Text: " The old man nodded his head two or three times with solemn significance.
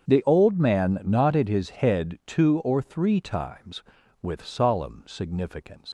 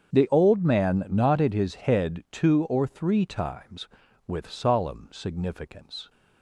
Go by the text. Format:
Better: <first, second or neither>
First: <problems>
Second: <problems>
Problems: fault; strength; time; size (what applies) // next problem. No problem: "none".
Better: second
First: starts louder than the rest; strong; until 1.0 s; 7.5 dB // leaves "significance" unfinished; at 5.8 s; 125 ms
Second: starts louder than the rest; strong; until 1.1 s; 7.5 dB